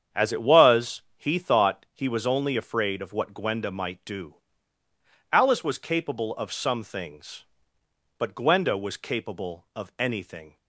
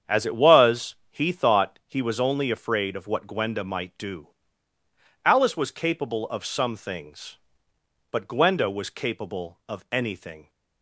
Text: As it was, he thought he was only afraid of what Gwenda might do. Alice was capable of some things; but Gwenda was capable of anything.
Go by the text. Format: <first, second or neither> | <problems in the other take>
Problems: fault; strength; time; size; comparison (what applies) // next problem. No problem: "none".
neither | starts louder than the rest; strong; the same in both